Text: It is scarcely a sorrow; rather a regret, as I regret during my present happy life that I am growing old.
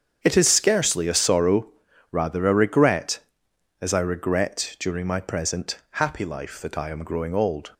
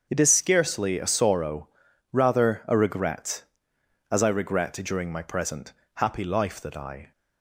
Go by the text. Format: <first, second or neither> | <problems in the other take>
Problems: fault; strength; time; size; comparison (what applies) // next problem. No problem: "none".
first | starts louder than the rest; until 1.1 s; 7 dB; strong in the first // pauses between "present" and "happy"; slight; at 5.7 s; 0.22 s long // stops before "am growing old"; at 7.1 s